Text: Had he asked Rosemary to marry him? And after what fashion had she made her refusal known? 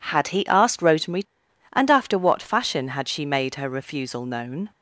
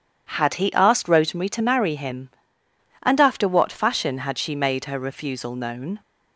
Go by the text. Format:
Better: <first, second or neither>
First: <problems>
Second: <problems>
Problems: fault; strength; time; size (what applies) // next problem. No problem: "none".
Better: second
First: skips "to marry him"; at 1.4 s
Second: none